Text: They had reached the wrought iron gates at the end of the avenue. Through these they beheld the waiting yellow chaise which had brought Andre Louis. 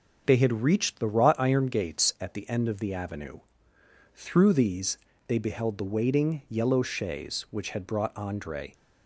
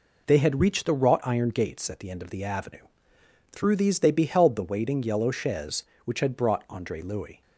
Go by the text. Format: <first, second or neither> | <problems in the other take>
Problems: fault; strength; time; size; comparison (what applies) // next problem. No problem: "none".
second | pauses between "these" and "they"; slight; at 4.9 s; 0.30 s long // stops before "Louis"; at 8.7 s